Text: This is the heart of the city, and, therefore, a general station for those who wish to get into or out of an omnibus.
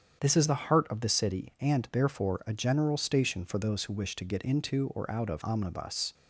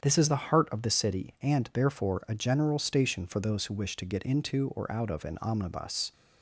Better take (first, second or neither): second